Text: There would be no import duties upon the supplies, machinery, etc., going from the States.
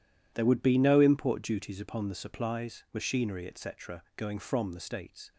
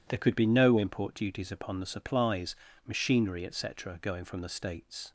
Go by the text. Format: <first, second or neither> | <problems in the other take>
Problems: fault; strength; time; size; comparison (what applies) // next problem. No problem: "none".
first | says "could" for "would"; at 0.1 s